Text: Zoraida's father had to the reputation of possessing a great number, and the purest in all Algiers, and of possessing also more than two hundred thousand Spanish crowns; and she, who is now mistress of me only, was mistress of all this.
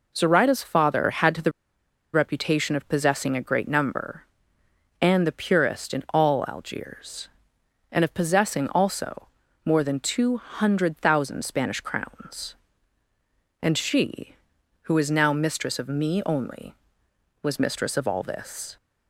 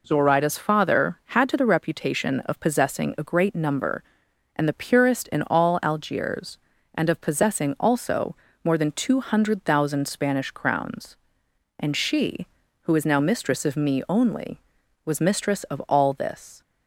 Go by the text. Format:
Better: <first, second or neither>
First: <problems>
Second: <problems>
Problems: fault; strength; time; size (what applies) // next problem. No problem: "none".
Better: second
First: pauses between "the" and "reputation"; noticeable; at 1.5 s; 0.62 s long // pauses between "also" and "more"; slight; at 9.2 s; 0.36 s long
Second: pauses between "also" and "more"; slight; at 8.3 s; 0.26 s long